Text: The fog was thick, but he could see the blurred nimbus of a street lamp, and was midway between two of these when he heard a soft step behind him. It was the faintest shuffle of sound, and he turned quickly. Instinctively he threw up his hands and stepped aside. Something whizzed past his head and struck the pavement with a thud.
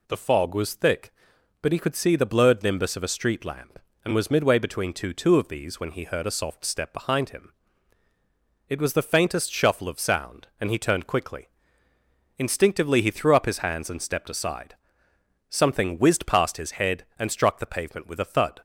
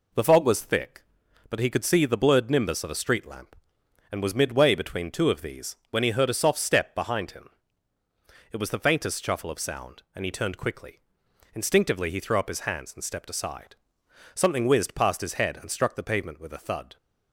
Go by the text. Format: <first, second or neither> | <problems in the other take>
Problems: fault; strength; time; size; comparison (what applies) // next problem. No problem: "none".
second | says "two" twice; at 5.1 s